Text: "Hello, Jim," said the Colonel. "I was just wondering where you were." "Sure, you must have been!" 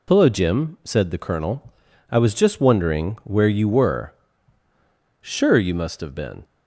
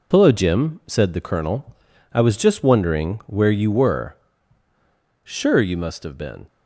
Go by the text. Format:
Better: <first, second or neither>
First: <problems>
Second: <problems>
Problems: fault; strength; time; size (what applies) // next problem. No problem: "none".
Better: first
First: none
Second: gets quieter; throughout; 6.5 dB